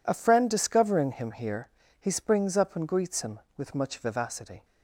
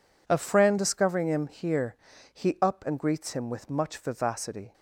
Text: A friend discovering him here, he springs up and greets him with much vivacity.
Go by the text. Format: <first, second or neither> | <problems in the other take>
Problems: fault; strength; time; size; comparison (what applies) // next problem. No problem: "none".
first | skips "springs"; at 2.5 s